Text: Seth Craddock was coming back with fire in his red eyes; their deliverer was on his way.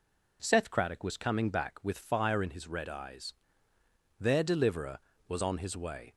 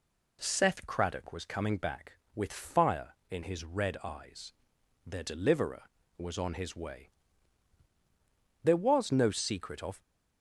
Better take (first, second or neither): first